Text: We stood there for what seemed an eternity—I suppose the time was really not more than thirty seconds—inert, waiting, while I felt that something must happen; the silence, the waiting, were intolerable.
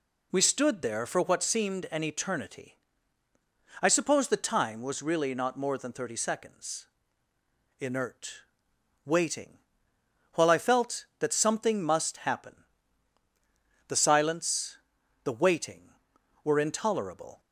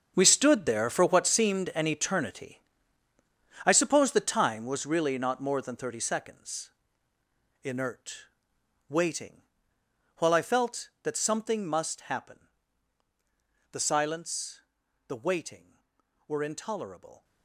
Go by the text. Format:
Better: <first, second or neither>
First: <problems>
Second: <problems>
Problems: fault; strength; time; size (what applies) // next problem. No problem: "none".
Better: first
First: none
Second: gets quieter; strong; throughout; 13.5 dB